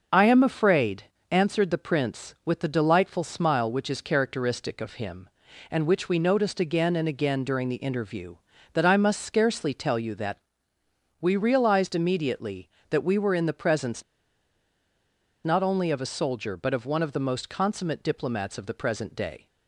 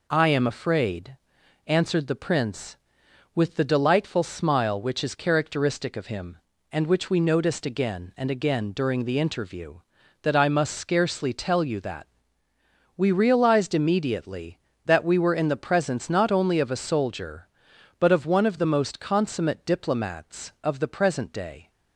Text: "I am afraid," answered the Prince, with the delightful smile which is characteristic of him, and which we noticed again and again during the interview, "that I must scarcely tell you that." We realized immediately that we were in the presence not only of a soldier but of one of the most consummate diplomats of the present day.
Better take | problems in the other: second | starts louder than the rest; until 1.4 s; 6.5 dB // pauses between "presence" and "not"; strong; at 14.0 s; 1.4 s long

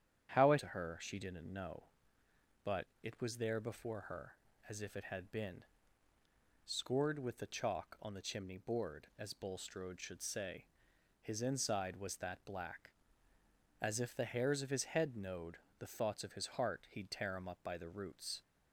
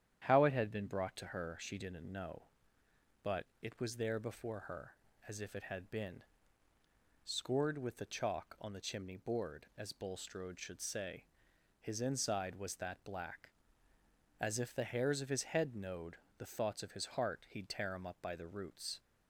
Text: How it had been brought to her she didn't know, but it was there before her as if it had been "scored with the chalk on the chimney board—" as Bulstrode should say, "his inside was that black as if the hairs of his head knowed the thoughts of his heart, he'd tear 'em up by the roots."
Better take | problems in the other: second | starts louder than the rest; strong; until 1.3 s; 9 dB; strong in the second // skips "had been brought"; at 0.5 s // pauses between "but" and "it"; slight; at 2.8 s; 0.18 s long; slight in the second // pauses between "been" and "scored"; at 5.6 s; 1.0 s long; also in the second // pauses between "knowed" and "the"; slight; at 15.5 s; 0.18 s long; slight in the second

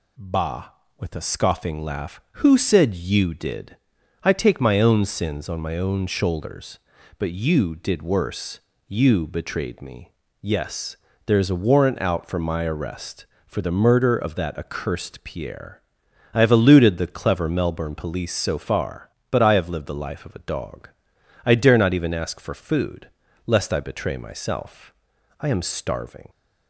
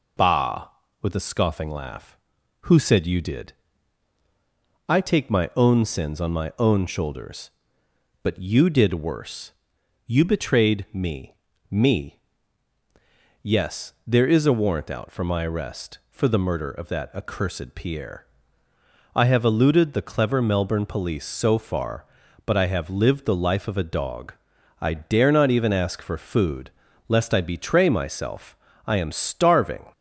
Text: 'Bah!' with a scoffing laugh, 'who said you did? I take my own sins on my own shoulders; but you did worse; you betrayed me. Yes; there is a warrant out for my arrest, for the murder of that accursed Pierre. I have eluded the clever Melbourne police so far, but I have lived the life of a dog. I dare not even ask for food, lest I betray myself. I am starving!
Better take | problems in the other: first | says "me" twice; at 11.6 s

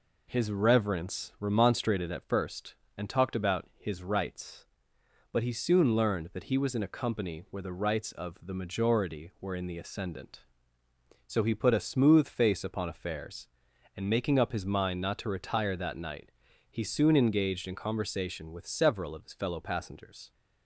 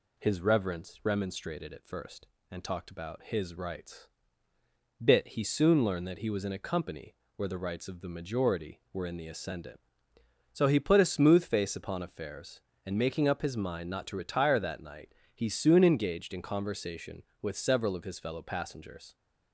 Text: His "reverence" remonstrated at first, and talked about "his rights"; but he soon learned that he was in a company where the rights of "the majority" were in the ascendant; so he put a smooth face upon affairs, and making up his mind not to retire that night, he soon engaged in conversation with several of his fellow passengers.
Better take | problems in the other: first | says "bit" for "but"; at 5.0 s // pauses between "company" and "where"; slight; at 7.1 s; 0.22 s long

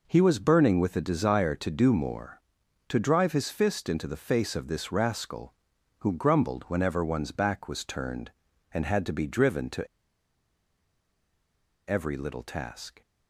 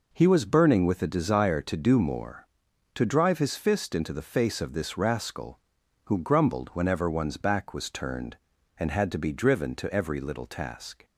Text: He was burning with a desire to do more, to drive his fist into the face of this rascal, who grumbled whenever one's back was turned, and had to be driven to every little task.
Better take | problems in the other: second | pauses between "to" and "every"; strong; at 9.8 s; 2.0 s long

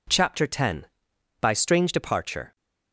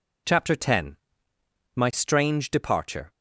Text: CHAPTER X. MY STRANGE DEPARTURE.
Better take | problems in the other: second | says "By" for "MY"; at 1.4 s

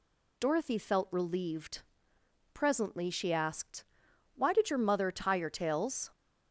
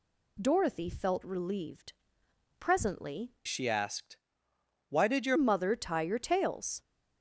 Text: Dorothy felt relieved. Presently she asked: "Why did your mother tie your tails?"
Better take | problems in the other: first | changes voice from "she" to "your"; from 3.4 to 5.3 s; 1.9 s long

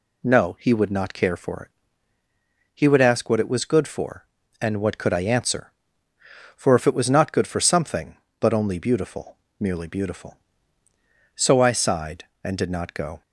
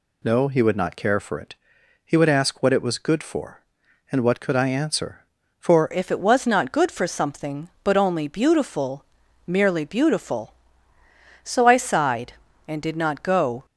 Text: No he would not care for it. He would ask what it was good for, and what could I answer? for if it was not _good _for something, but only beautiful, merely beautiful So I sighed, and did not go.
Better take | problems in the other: first | changes voice at "if"; from 5.9 s on; 7.7 s long

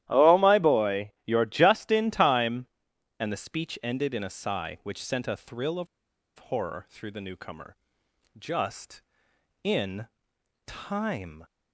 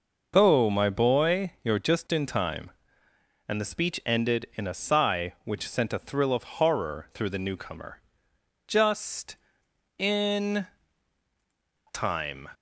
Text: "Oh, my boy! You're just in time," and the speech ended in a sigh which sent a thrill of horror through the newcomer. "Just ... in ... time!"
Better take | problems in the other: second | starts louder than the rest; strong; until 1.0 s; 13 dB // pauses between "of" and "horror"; noticeable; at 5.8 s; 0.51 s long

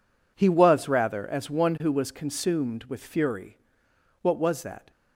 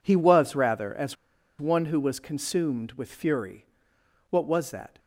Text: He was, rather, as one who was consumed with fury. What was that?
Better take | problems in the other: first | pauses between "as" and "one"; at 1.1 s; 0.43 s long

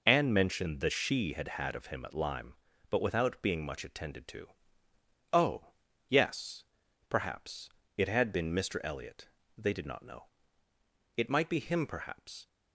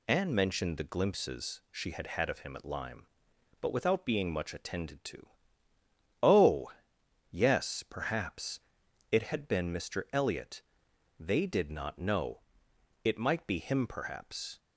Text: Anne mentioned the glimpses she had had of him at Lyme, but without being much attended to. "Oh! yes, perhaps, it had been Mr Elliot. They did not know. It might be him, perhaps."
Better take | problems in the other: second | skips "glimpses"; at 0.8 s

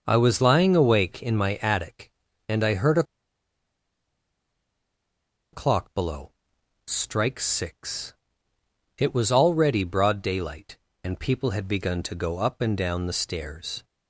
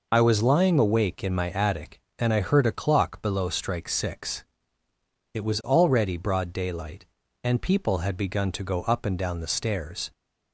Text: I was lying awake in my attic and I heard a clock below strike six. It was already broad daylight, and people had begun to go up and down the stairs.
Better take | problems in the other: second | starts louder than the rest; noticeable; until 1.0 s; 6 dB // pauses between "a" and "clock"; strong; at 3.0 s; 2.4 s long // pauses between "below" and "strike"; noticeable; at 6.3 s; 0.54 s long

